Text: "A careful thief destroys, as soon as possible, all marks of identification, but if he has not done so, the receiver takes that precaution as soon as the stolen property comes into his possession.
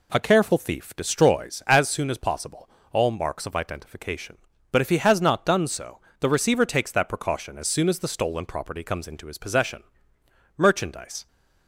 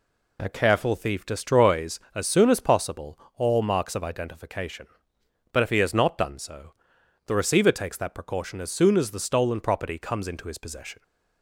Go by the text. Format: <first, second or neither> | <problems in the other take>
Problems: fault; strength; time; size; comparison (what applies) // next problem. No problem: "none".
second | goes on to say "Merchandise"; noticeable; from 10.5 s on; 0.70 s long